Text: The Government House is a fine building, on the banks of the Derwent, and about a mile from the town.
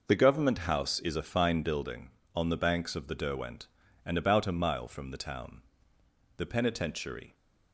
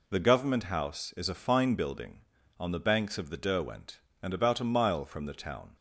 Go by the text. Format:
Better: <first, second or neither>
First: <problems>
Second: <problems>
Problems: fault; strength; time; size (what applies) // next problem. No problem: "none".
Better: second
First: goes on to say "The Penitentiary"; noticeable; from 6.3 s on; 0.98 s long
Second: none